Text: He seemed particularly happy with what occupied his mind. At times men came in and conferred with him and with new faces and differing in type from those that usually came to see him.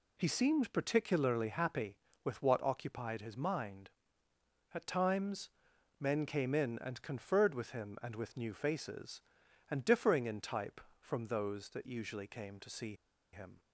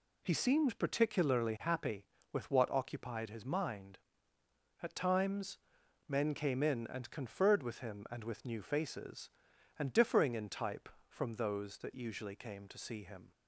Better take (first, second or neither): second